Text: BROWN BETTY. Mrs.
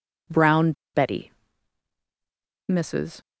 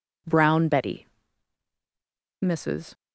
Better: second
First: pauses between "BROWN" and "BETTY"; slight; at 0.7 s; 0.22 s long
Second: none

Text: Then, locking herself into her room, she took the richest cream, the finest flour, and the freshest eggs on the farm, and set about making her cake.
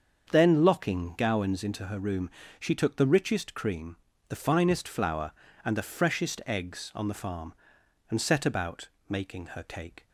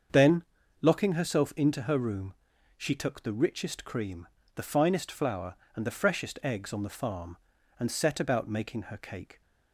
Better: second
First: starts louder than the rest; until 1.3 s; 7 dB // says "gowans" for "herself"; at 1.1 s // pauses between "about" and "making"; slight; at 8.8 s; 0.20 s long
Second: starts louder than the rest; until 1.4 s; 7 dB

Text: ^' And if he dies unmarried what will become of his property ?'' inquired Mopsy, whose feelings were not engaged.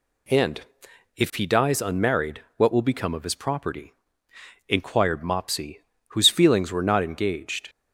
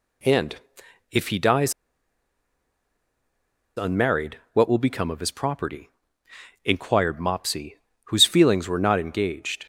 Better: first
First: pauses between "And" and "if"; noticeable; at 0.5 s; 0.56 s long // pauses between "unmarried" and "what"; slight; at 2.4 s; 0.16 s long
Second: pauses between "And" and "if"; noticeable; at 0.5 s; 0.56 s long // pauses between "dies" and "unmarried"; strong; at 1.7 s; 2.0 s long // pauses between "unmarried" and "what"; slight; at 4.3 s; 0.16 s long

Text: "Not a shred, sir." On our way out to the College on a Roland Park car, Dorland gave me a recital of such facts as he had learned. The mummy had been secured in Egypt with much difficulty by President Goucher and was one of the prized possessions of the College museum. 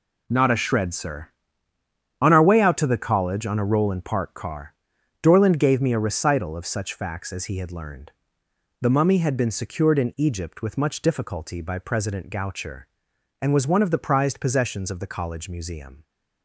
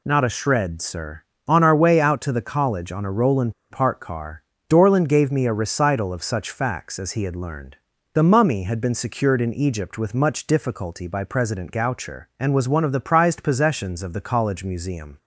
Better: first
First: none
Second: pauses between "Roland" and "Park"; slight; at 3.5 s; 0.18 s long

